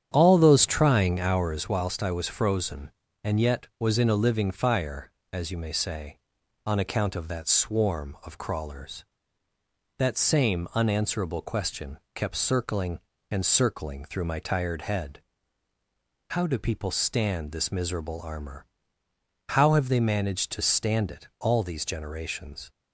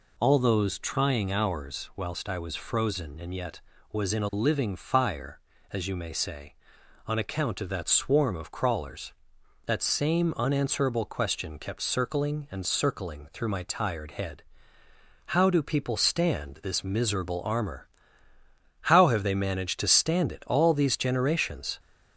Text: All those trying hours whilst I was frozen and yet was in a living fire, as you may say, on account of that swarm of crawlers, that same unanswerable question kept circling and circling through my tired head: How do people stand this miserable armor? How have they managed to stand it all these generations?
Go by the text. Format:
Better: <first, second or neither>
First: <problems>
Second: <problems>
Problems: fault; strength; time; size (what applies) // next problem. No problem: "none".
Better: second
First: starts louder than the rest; strong; until 1.7 s; 9 dB // pauses between "question" and "kept"; slight; at 11.9 s; 0.16 s long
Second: none